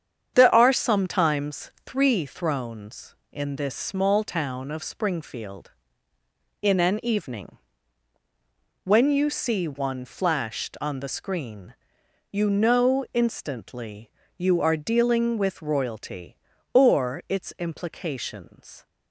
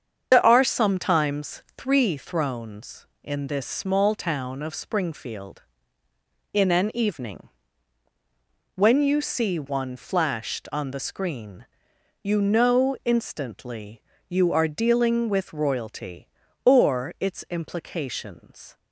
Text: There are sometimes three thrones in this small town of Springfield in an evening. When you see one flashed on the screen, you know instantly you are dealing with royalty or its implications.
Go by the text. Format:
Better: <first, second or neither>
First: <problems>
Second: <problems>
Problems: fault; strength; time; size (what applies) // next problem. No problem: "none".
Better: first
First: starts louder than the rest; strong; until 1.3 s; 8.5 dB // pauses between "sometimes" and "three"; slight; at 1.6 s; 0.16 s long // pauses between "instantly" and "you"; slight; at 14.0 s; 0.26 s long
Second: loses the start of "There"; at 0.3 s; 50 ms // starts louder than the rest; strong; until 1.3 s; 7.5 dB // pauses between "sometimes" and "three"; slight; at 1.6 s; 0.16 s long // pauses between "instantly" and "you"; slight; at 14.0 s; 0.26 s long